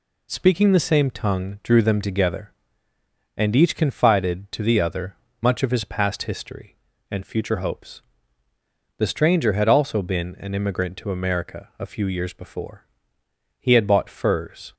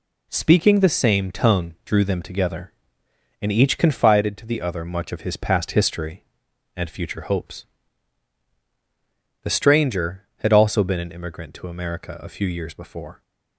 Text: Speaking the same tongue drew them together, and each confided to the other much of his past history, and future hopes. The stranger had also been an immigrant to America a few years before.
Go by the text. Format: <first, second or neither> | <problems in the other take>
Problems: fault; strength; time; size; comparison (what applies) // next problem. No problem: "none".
second | pauses between "other" and "much"; slight; at 5.1 s; 0.26 s long // goes on to say "He had bought furs"; noticeable; from 13.5 s on; 1.1 s long